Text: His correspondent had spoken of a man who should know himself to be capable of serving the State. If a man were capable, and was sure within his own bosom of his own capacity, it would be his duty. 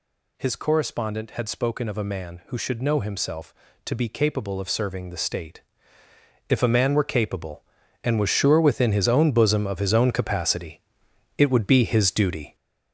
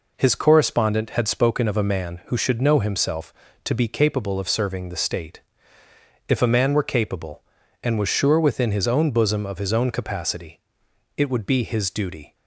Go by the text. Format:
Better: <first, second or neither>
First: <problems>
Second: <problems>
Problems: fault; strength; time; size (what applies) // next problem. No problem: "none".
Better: second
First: gets louder; throughout; 6 dB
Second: none